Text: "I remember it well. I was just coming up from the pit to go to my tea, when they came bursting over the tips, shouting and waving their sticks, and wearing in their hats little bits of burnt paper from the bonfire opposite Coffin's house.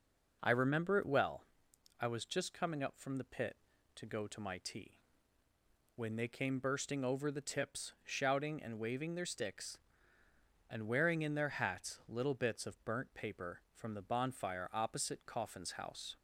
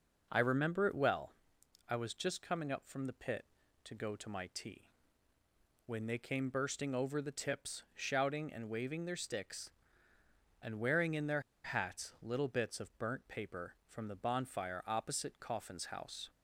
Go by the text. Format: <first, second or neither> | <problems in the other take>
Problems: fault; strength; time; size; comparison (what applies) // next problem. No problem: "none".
first | pauses between "their" and "hats"; slight; at 11.4 s; 0.23 s long